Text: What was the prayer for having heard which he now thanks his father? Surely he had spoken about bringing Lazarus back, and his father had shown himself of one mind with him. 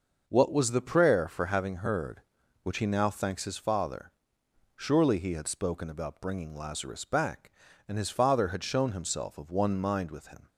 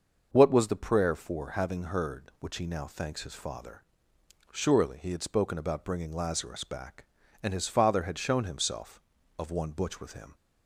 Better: first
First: none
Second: starts louder than the rest; noticeable; until 1.3 s; 6 dB // says "butch" for "mind"; at 9.7 s

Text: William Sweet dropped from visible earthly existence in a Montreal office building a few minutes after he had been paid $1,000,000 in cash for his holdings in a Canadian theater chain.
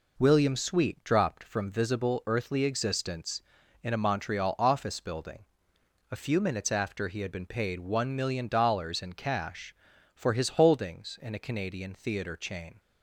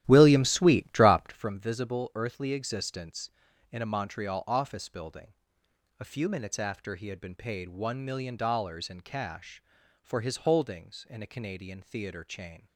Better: first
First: pauses between "building" and "a"; noticeable; at 5.4 s; 0.64 s long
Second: starts louder than the rest; strong; until 1.6 s; 13 dB // pauses between "building" and "a"; noticeable; at 5.3 s; 0.64 s long

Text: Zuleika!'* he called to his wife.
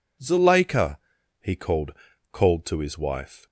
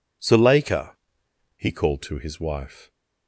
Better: second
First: says "called" twice; at 2.3 s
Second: none

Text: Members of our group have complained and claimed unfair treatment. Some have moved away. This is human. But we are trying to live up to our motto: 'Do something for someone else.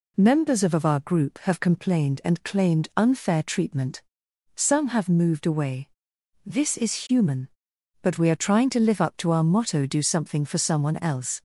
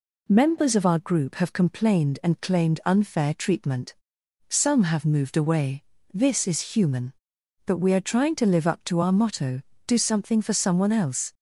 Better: second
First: says "of" twice; at 0.7 s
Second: none

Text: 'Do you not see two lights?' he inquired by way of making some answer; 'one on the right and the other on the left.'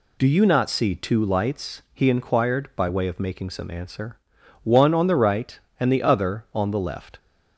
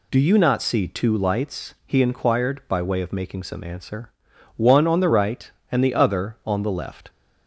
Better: neither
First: none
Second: none

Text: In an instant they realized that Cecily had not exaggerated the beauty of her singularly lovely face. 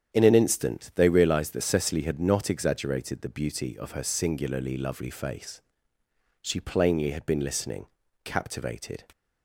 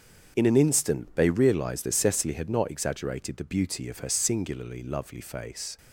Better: second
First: starts louder than the rest; strong; until 1.2 s; 9 dB // goes on to say "She plainly had been listening captivated"; strong; from 6.4 s on; 2.6 s long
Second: starts louder than the rest; until 1.3 s; 7 dB

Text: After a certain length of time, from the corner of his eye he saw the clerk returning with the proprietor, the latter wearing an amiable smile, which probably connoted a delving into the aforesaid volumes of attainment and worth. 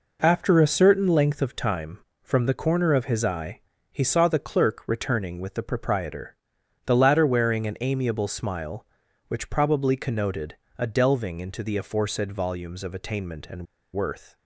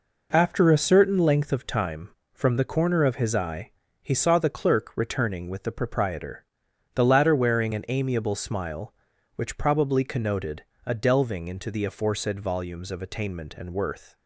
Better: second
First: pauses between "eye" and "he"; slight; at 3.6 s; 0.30 s long // pauses between "connoted" and "a"; slight; at 10.5 s; 0.20 s long // pauses between "and" and "worth"; slight; at 13.6 s; 0.28 s long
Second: pauses between "eye" and "he"; slight; at 3.7 s; 0.30 s long // pauses between "connoted" and "a"; slight; at 10.6 s; 0.20 s long

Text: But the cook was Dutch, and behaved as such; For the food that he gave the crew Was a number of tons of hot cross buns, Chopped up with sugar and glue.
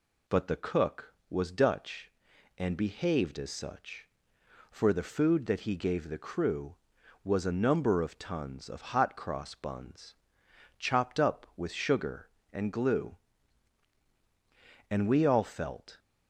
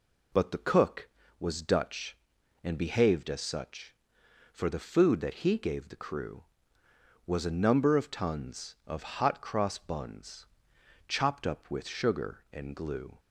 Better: second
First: goes on to say "And we all felt"; noticeable; from 14.9 s on; 1.0 s long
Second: none

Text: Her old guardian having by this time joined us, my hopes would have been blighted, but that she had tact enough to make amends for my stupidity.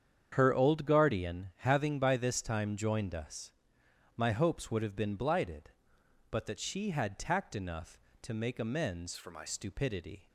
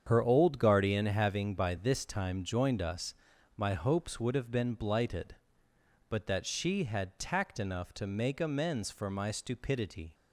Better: second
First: starts louder than the rest; strong; until 1.3 s; 8 dB // changes voice from "for" to "my"; from 9.1 to 9.4 s; 0.3 s long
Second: starts louder than the rest; strong; until 1.0 s; 7.5 dB

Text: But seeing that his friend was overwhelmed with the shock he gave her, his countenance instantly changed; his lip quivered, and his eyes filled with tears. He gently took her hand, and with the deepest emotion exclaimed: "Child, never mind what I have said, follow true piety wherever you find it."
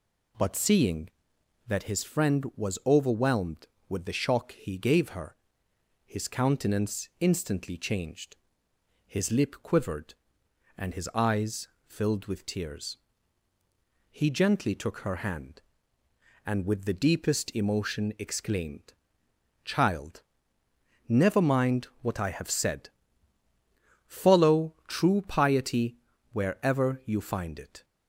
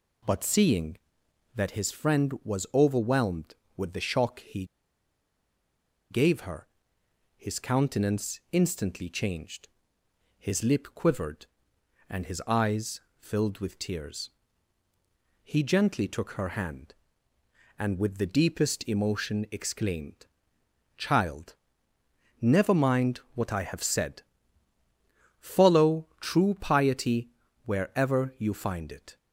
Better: first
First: pauses between "eyes" and "filled"; slight; at 11.6 s; 0.18 s long // pauses between "mind" and "what"; slight; at 21.8 s; 0.16 s long // pauses between "piety" and "wherever"; slight; at 25.9 s; 0.36 s long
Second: pauses between "he" and "gave"; strong; at 4.6 s; 1.4 s long // pauses between "eyes" and "filled"; slight; at 13.0 s; 0.18 s long // pauses between "mind" and "what"; slight; at 23.1 s; 0.16 s long // pauses between "piety" and "wherever"; slight; at 27.2 s; 0.36 s long

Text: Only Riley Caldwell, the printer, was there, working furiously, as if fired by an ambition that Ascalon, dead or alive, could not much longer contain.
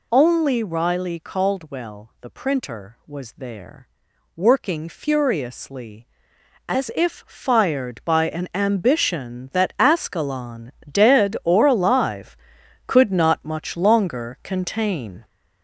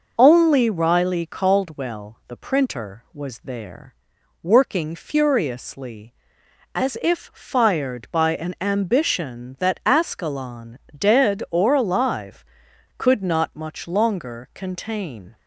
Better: second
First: gets louder; noticeable; throughout; 5 dB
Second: none

